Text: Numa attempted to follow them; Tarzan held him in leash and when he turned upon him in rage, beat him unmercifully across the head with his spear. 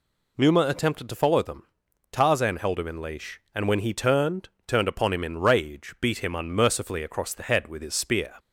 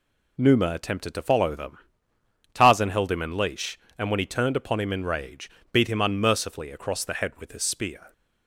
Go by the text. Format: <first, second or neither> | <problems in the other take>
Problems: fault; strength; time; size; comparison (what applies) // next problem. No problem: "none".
second | says "turned" twice; at 4.6 s